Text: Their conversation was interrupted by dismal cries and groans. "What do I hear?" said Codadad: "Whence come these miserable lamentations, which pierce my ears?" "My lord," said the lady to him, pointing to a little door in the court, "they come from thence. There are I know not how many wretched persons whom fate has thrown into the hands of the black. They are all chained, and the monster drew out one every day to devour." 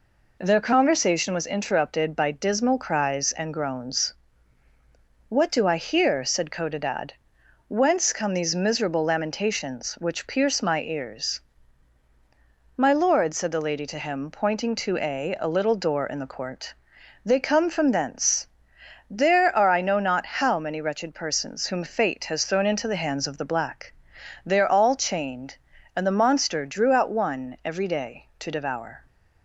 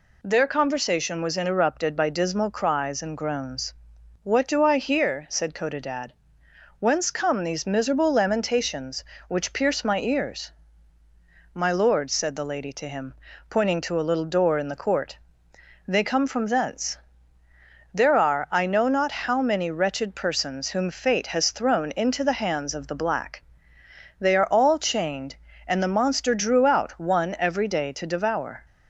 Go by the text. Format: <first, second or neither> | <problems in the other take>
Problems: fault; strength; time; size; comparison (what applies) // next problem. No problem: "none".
second | says "a" twice; at 15.3 s